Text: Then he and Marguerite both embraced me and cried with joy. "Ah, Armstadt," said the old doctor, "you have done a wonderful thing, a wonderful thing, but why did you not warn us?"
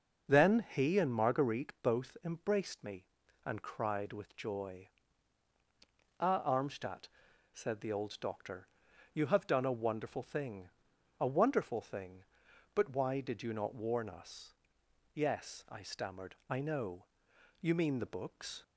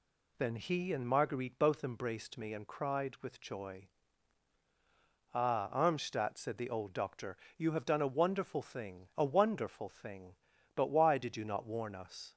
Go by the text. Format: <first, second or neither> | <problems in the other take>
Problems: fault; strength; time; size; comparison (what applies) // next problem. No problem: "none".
second | starts louder than the rest; noticeable; until 1.3 s; 6 dB // goes on to say "Yes I stammered I know You mean the books"; strong; from 15.1 s on; 3.5 s long